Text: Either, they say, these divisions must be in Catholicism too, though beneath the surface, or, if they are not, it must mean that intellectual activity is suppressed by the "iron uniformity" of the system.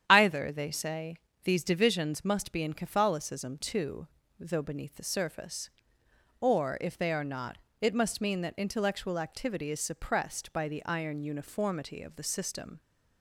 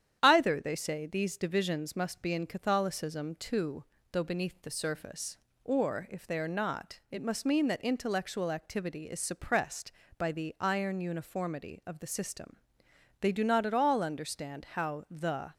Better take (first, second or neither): first